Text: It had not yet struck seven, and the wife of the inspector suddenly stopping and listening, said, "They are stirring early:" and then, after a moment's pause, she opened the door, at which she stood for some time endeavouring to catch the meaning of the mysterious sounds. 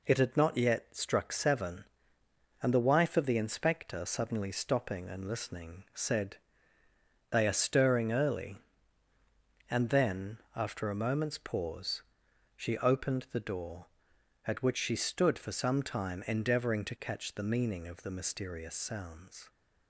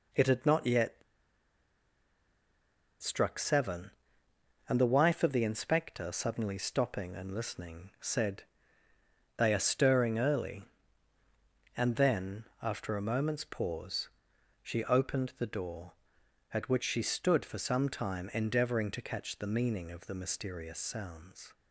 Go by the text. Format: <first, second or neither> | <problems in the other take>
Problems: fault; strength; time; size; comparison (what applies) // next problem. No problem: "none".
first | pauses between "yet" and "struck"; strong; at 1.0 s; 2.0 s long